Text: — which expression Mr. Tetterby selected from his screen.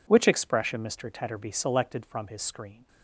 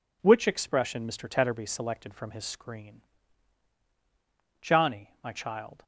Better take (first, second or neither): first